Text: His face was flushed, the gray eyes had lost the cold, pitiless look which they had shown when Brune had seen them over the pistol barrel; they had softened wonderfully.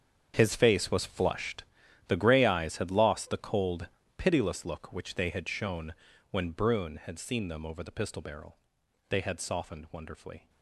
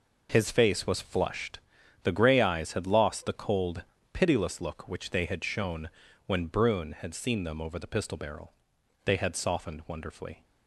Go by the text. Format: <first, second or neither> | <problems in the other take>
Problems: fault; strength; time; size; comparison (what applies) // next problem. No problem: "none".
second | gets quieter; strong; throughout; 15 dB // pauses between "shown" and "when"; at 5.9 s; 0.38 s long; also in the second